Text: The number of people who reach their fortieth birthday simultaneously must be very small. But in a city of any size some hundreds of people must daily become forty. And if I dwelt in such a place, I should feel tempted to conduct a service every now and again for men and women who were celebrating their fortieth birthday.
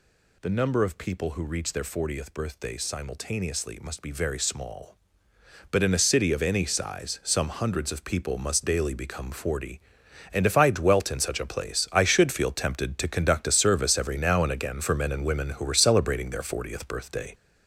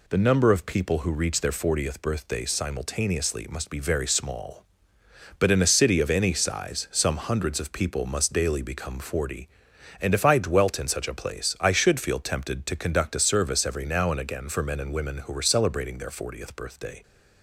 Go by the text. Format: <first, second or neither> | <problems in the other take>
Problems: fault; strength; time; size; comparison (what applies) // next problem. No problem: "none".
second | gets louder; noticeable; throughout; 5 dB